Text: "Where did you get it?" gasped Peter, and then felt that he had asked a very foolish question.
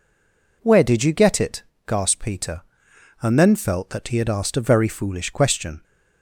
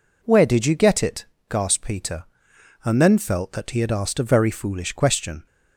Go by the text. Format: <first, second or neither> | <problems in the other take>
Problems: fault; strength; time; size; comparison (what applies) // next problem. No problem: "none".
second | stays silent before the first word; slight; until 0.6 s; 0.6 s long